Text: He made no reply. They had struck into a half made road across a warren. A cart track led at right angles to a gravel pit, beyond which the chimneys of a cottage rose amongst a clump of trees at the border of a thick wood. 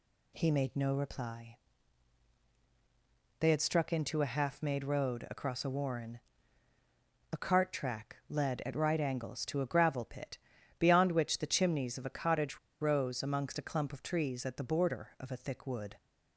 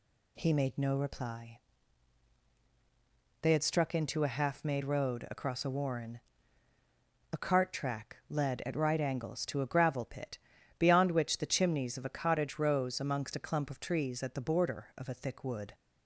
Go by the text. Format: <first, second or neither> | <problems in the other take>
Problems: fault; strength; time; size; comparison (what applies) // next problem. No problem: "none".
second | pauses between "cottage" and "rose"; slight; at 12.5 s; 0.22 s long